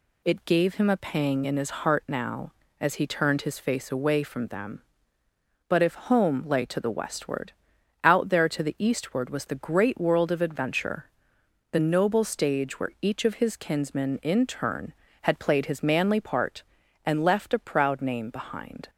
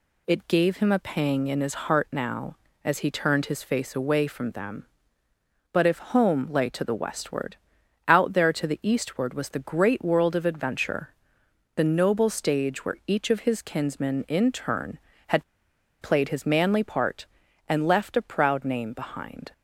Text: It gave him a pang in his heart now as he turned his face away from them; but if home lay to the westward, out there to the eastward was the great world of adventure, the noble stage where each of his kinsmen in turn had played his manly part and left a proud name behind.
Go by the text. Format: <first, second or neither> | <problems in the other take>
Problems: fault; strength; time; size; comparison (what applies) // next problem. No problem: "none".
first | pauses between "had" and "played"; noticeable; at 15.4 s; 0.58 s long